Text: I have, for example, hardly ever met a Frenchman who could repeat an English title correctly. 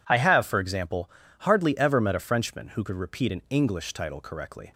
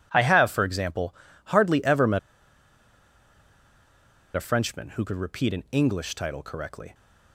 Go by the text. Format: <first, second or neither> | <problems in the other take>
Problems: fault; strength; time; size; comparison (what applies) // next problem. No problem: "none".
first | pauses between "met" and "a"; strong; at 2.1 s; 2.1 s long